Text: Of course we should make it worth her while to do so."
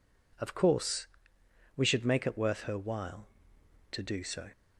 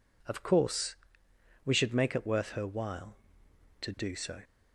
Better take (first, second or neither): neither